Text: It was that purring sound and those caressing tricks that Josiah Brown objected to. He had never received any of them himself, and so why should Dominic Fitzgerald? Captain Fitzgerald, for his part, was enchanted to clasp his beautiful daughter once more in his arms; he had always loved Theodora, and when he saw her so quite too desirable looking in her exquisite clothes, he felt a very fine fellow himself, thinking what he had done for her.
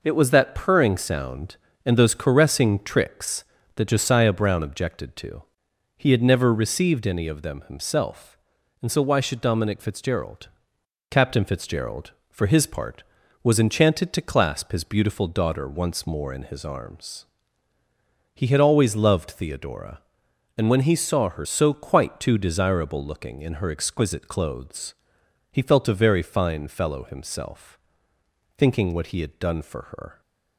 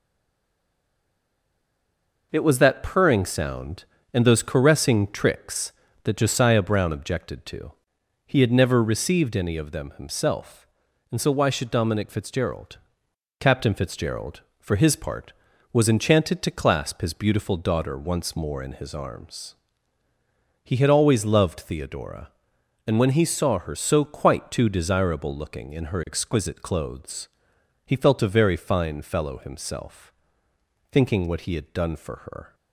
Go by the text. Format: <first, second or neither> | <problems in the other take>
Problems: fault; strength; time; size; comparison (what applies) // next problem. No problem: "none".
first | stays silent before the first word; until 2.3 s; 2.3 s long